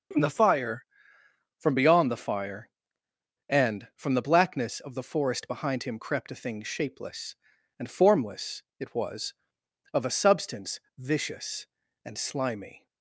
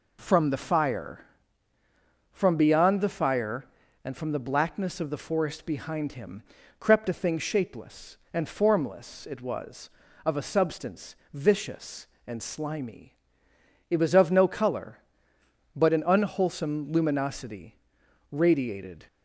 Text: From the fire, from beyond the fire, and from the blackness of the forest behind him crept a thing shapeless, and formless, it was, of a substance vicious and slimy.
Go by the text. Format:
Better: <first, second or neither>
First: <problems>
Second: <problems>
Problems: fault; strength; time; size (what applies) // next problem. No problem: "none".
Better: first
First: pauses between "substance" and "vicious"; slight; at 10.7 s; 0.18 s long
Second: pauses between "him" and "crept"; slight; at 6.4 s; 0.36 s long // pauses between "substance" and "vicious"; slight; at 11.1 s; 0.18 s long // goes on to say "It was of no color but an unwholesome luminosity radiated"; strong; from 13.8 s on; 5.1 s long